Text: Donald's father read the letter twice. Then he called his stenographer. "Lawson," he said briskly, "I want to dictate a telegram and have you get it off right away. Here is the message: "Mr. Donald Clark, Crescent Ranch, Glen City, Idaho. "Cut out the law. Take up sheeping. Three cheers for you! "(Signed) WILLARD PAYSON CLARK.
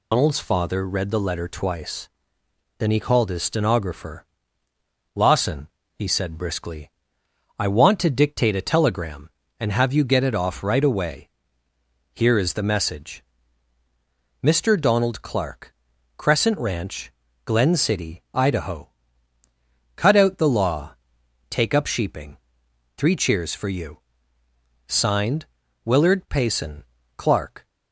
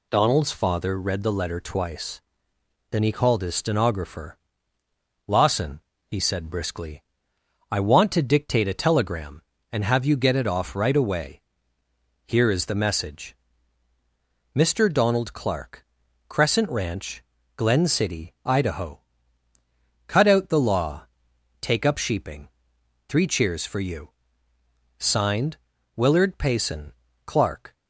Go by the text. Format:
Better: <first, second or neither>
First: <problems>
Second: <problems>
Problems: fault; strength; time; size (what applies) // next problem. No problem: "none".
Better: second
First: loses the start of "Donald's"; at 0.1 s; 135 ms // pauses between "PAYSON" and "CLARK"; slight; at 26.8 s; 0.32 s long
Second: pauses between "PAYSON" and "CLARK"; slight; at 26.9 s; 0.32 s long